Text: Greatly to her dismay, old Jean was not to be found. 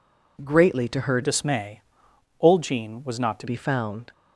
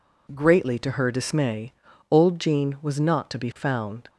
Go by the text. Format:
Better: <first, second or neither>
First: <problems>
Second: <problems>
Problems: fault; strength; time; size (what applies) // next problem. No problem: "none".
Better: second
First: changes voice from "dismay" to "to"; from 1.2 to 3.4 s; 2.2 s long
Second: none